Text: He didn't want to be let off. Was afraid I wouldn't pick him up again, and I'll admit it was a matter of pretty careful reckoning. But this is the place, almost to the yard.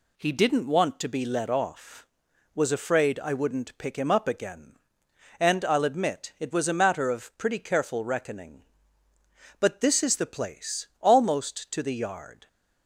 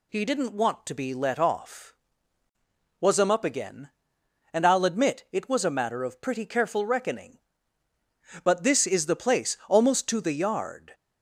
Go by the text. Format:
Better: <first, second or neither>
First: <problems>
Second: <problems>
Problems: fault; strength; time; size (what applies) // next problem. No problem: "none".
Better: first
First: none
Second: skips "afraid I wouldn't pick"; at 3.2 s